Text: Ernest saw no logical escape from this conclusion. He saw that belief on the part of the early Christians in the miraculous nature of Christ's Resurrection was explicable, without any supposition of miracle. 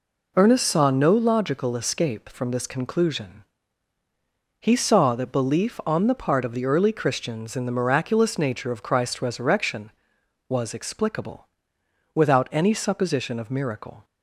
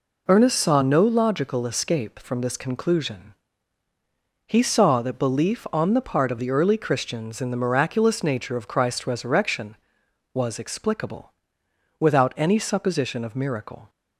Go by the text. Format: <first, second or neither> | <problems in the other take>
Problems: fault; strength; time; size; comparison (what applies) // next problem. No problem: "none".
neither | none